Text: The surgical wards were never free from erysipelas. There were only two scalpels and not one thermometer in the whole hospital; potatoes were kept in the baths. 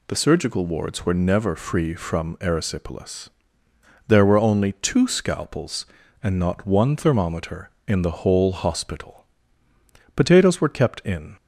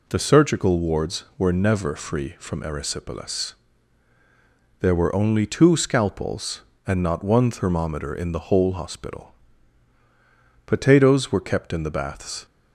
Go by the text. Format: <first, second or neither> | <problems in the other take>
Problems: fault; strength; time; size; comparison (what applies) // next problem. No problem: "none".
second | stops before "the baths"; at 11.3 s